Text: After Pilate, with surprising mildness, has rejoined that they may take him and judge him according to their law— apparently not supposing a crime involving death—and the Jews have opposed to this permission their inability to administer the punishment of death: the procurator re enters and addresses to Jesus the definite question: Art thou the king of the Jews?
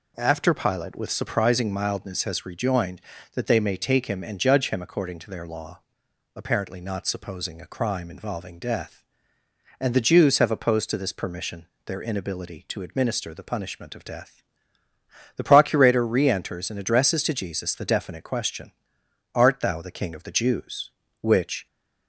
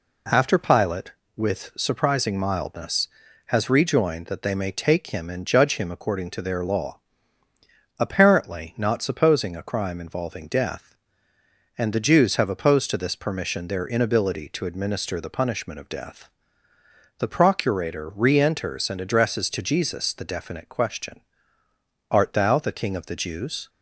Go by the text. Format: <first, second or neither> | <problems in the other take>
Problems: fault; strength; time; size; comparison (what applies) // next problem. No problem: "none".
second | pauses between "permission" and "their"; slight; at 11.6 s; 0.20 s long // goes on to say "which"; slight; from 21.2 s on; 0.44 s long